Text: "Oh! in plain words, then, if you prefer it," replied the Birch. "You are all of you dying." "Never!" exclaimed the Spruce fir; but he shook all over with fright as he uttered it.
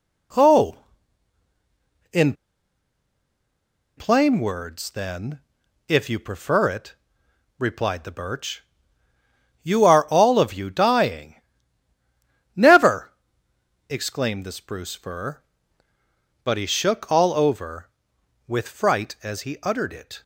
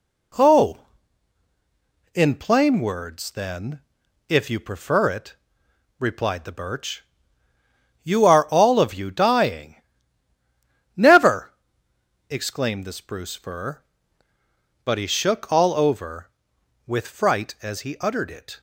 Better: second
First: pauses between "in" and "plain"; strong; at 2.3 s; 1.6 s long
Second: none

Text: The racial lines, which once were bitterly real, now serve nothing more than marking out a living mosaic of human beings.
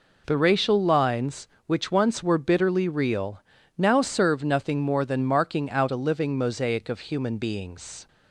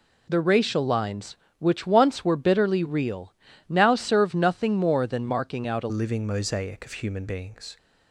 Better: first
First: none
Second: changes voice at "living"; from 5.9 s on; 1.8 s long

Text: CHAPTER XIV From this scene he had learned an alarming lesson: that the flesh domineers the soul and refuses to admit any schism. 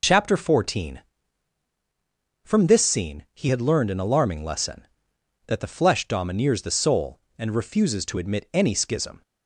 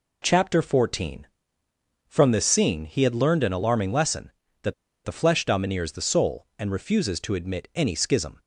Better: first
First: none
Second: pauses between "that" and "the"; slight; at 4.7 s; 0.31 s long

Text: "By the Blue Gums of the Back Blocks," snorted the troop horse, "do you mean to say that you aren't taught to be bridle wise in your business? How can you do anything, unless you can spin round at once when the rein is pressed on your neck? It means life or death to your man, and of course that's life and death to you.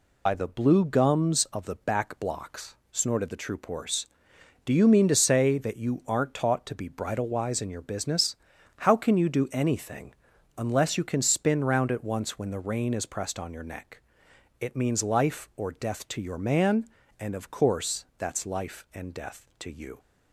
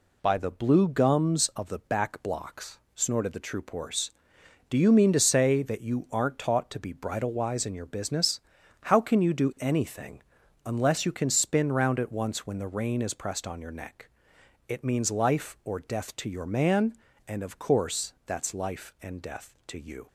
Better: second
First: loses the start of "By"; at 0.2 s; 70 ms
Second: none

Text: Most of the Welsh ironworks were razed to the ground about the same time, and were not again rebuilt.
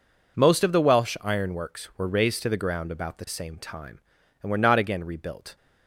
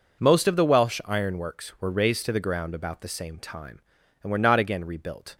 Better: neither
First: none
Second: none

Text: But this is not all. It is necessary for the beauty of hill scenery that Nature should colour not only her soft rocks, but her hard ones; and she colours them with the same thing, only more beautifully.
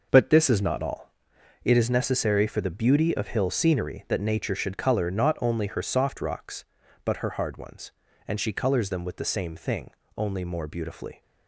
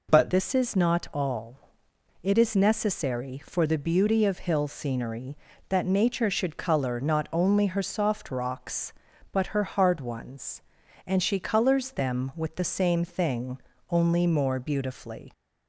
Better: first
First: none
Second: changes voice at "this"; from 0.2 s on; 15.1 s long

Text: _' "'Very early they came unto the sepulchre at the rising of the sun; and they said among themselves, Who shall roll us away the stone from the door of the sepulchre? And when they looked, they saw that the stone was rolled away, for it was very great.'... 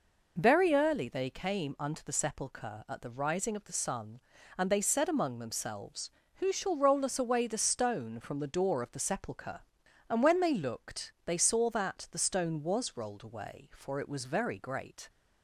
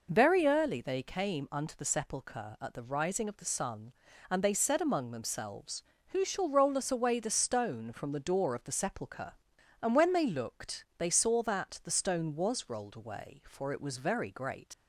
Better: first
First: none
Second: leaves "great" unfinished; at 14.7 s; 80 ms

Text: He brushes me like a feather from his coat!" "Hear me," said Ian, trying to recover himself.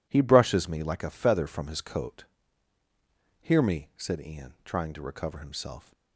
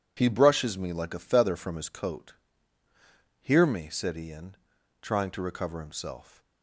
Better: neither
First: none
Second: none

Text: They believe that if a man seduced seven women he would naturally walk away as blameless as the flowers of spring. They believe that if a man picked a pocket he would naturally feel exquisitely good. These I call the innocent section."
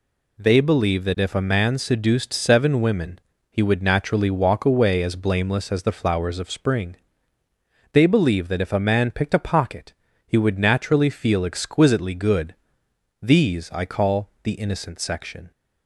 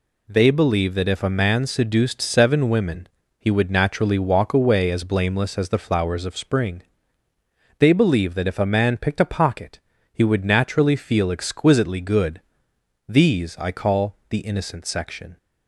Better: neither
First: pauses between "women" and "he"; slight; at 3.1 s; 0.32 s long // pauses between "pocket" and "he"; slight; at 9.9 s; 0.32 s long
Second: pauses between "women" and "he"; slight; at 3.0 s; 0.32 s long // pauses between "pocket" and "he"; slight; at 9.7 s; 0.32 s long

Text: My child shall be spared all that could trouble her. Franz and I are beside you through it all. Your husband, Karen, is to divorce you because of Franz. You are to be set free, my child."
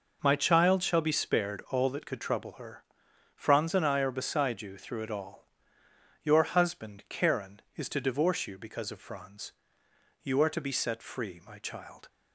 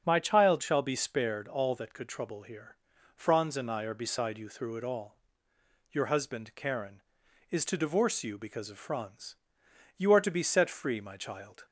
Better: first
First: none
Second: starts louder than the rest; strong; until 1.0 s; 7 dB // says "here" for "her"; at 2.4 s

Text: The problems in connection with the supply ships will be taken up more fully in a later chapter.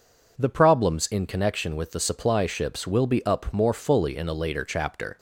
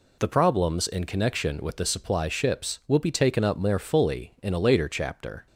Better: second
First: skips "taken"; at 3.2 s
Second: none

